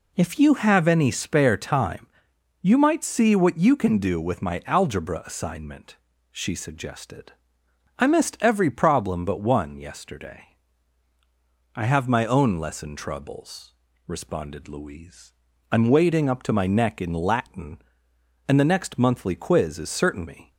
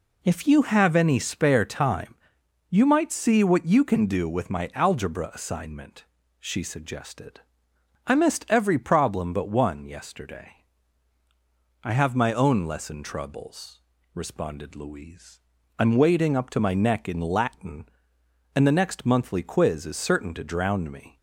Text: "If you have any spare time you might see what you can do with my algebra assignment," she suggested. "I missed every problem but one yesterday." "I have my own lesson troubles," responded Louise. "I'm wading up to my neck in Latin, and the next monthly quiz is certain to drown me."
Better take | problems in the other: second | pauses between "time" and "you"; noticeable; at 2.0 s; 0.56 s long; noticeable in the second // skips "to drown"; at 20.2 s

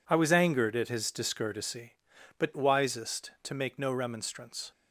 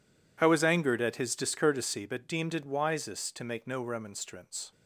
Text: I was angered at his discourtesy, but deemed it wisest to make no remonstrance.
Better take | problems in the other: second | skips "deemed it"; at 2.5 s

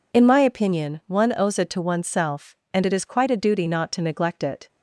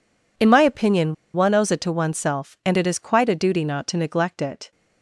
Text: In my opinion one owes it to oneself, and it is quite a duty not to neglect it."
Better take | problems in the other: first | pauses between "opinion" and "one"; slight; at 1.1 s; 0.20 s long

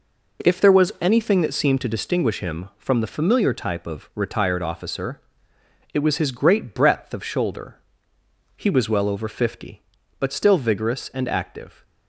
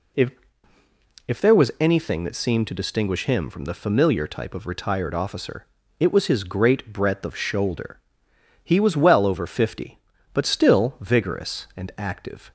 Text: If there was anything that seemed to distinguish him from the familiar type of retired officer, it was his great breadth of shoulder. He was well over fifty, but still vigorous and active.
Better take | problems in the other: first | says "If" twice; at 1.2 s

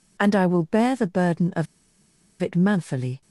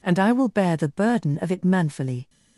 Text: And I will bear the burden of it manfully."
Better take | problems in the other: second | pauses between "of" and "it"; noticeable; at 1.6 s; 0.75 s long

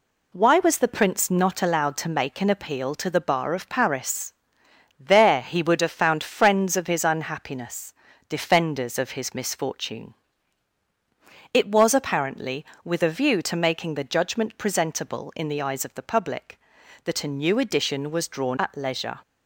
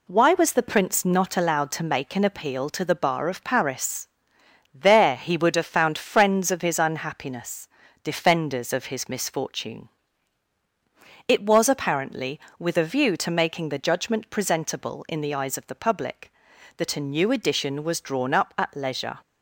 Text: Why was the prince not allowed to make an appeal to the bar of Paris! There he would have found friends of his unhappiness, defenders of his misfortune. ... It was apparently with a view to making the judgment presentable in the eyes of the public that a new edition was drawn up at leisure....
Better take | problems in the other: second | skips "up"; at 18.5 s

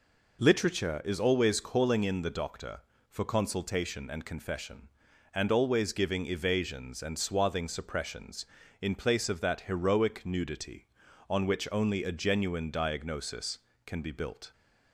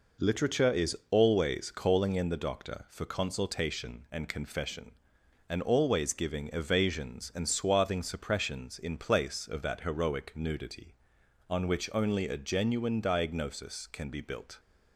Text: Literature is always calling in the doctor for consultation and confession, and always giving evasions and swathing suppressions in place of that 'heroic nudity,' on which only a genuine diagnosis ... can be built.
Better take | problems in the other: neither | none

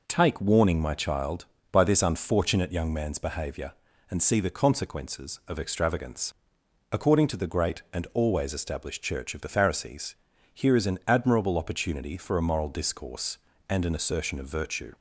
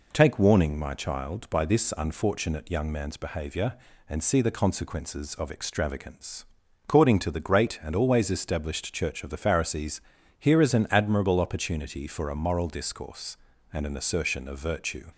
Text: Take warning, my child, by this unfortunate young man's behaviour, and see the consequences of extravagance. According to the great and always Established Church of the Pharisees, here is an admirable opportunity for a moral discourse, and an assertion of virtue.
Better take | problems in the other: neither | none

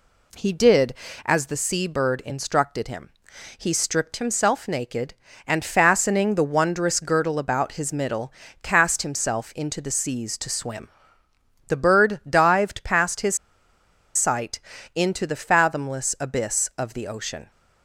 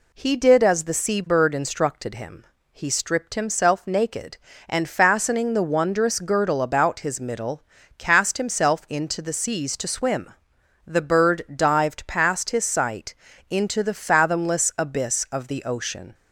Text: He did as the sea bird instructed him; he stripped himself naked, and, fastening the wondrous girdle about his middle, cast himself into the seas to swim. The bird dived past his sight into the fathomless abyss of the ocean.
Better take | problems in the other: second | pauses between "his" and "sight"; noticeable; at 13.3 s; 0.79 s long // pauses between "sight" and "into"; slight; at 14.5 s; 0.34 s long; slight in the second

